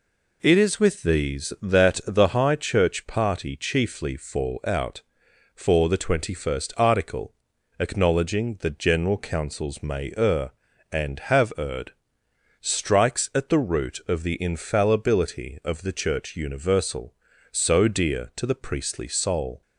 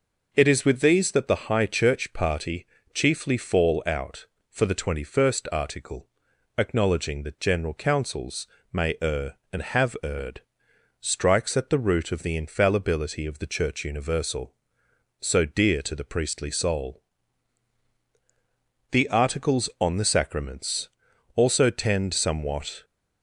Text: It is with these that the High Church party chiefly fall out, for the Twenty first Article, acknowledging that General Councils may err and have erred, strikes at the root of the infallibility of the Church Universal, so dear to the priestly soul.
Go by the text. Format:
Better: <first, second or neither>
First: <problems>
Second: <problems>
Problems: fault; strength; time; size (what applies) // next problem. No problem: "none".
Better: first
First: none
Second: pauses between "party" and "chiefly"; slight; at 2.6 s; 0.28 s long // pauses between "Councils" and "may"; slight; at 8.4 s; 0.24 s long // goes on to say "The Articles on the Sacraments also tend somewhat"; strong; from 18.9 s on; 3.9 s long